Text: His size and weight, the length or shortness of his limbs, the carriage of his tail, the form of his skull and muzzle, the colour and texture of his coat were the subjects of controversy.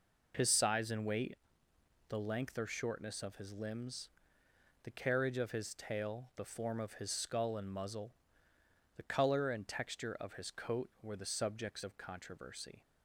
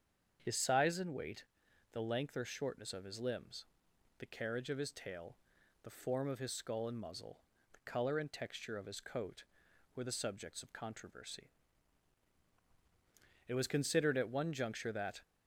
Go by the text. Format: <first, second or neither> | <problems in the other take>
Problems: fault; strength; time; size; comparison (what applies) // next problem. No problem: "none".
first | starts louder than the rest; strong; until 1.4 s; 7.5 dB // goes on to say "It was considered at one juncture that"; strong; from 13.4 s on; 1.7 s long